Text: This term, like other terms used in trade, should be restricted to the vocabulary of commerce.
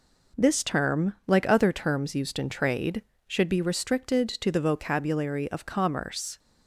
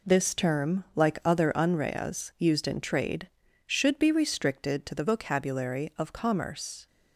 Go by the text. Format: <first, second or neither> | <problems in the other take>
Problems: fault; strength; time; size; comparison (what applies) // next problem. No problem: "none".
first | says "unreas" for "terms"; at 1.5 s